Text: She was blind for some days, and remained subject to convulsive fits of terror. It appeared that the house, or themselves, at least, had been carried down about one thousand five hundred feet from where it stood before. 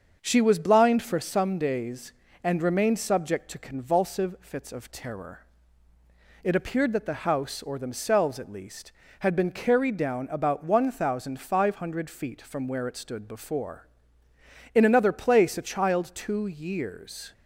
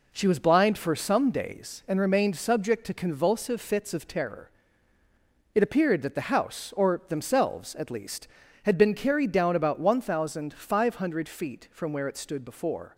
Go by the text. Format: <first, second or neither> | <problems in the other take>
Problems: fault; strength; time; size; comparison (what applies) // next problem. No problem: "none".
second | starts louder than the rest; until 1.2 s; 6.5 dB // goes on to say "In another place a child two years"; strong; from 14.7 s on; 2.5 s long